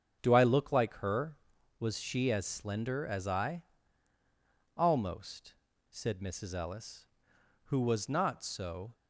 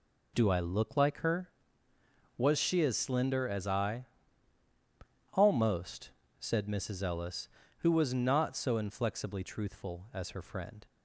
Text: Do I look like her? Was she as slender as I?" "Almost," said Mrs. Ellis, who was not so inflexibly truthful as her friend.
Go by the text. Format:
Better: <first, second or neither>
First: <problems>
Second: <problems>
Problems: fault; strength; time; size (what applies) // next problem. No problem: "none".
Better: second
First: starts louder than the rest; until 1.2 s; 7 dB // stops before "inflexibly truthful as her friend"; at 8.9 s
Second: none